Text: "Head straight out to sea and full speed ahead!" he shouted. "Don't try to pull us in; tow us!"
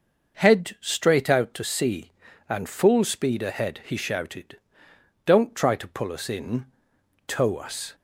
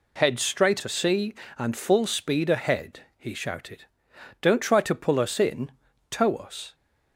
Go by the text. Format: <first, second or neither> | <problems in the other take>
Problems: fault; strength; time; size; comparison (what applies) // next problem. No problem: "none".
first | skips "out"; at 0.7 s